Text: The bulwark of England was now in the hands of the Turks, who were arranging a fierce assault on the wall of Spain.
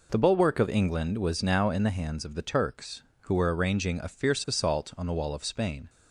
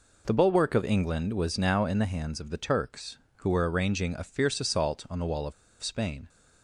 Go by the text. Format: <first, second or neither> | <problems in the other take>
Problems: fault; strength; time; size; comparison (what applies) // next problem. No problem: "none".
first | pauses between "of" and "Spain"; slight; at 5.5 s; 0.29 s long